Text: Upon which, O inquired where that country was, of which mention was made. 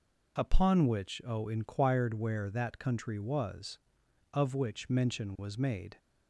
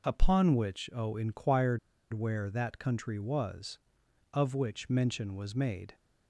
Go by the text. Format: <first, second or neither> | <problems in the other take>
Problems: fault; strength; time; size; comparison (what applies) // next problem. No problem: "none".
first | pauses between "inquired" and "where"; slight; at 1.7 s; 0.33 s long